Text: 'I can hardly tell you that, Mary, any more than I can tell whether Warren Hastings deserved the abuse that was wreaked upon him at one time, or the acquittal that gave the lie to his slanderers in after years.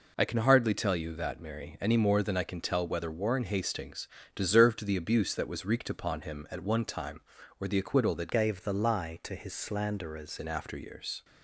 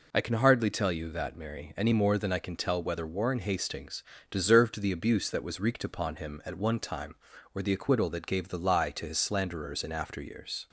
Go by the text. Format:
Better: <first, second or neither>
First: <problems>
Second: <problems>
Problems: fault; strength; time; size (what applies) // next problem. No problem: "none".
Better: second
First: pauses between "Hastings" and "deserved"; slight; at 4.0 s; 0.28 s long // changes voice from "gave" to "slanderers"; from 8.3 to 10.3 s; 2.0 s long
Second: pauses between "Hastings" and "deserved"; slight; at 4.0 s; 0.28 s long